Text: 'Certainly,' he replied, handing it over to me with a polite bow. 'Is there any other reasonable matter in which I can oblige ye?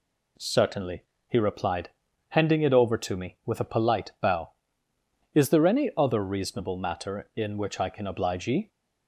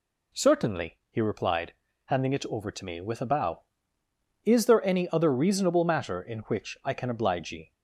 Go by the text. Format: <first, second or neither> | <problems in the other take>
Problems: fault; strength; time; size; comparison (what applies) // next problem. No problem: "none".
first | skips "polite"; at 3.2 s